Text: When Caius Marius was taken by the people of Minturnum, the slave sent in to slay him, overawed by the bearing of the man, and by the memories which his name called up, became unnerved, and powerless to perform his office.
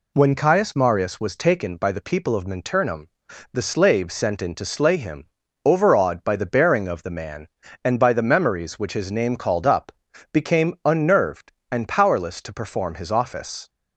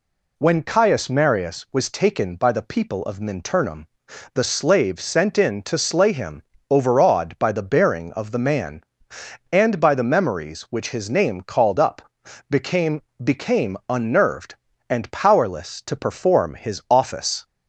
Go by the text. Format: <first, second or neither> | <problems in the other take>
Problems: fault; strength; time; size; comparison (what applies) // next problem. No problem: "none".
first | says "became" twice; at 13.2 s